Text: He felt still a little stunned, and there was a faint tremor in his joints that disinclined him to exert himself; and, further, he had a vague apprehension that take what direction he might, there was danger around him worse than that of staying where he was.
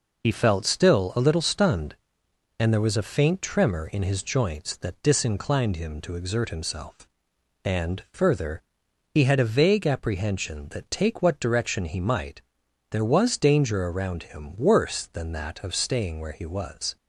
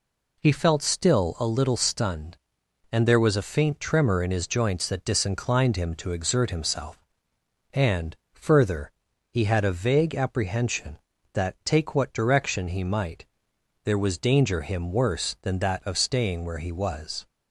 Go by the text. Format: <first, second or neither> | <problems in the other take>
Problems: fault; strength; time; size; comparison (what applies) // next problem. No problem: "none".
first | skips "around"; at 14.6 s